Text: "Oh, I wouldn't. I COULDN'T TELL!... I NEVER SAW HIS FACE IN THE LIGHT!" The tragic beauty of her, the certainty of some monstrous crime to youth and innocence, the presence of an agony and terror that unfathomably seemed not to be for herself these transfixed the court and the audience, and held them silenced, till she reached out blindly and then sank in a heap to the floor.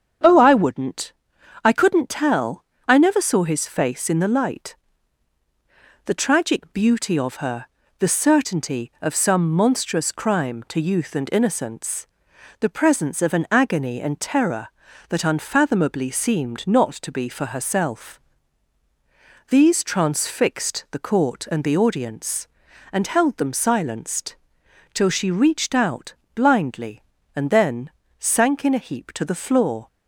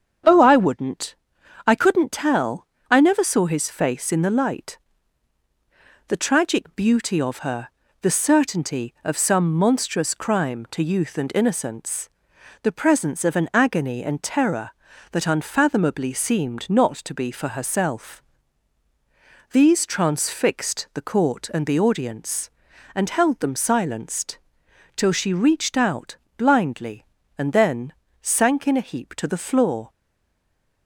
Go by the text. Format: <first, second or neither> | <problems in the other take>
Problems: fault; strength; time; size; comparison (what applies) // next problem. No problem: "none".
first | starts louder than the rest; strong; until 1.7 s; 7.5 dB; strong in the first // pauses between "herself" and "these"; strong; at 18.2 s; 1.3 s long; strong in the first // pauses between "out" and "blindly"; slight; at 26.1 s; 0.20 s long; slight in the first // pauses between "then" and "sank"; slight; at 27.9 s; 0.28 s long; slight in the first // stays silent after the last word; from 29.9 s on; 0.9 s long